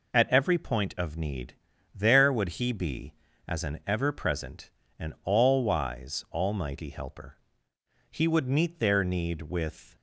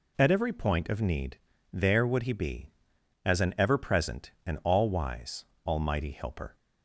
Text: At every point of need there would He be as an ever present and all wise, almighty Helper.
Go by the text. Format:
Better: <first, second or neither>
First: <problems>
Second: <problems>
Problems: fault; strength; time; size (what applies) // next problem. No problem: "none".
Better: second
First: pauses between "need" and "there"; at 1.5 s; 0.38 s long // goes on to say "He would meet their need with"; strong; from 8.0 s on; 1.8 s long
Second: pauses between "need" and "there"; slight; at 1.3 s; 0.34 s long